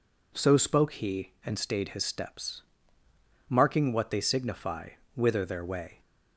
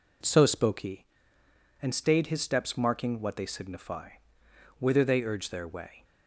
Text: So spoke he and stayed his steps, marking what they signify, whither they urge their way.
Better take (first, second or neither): second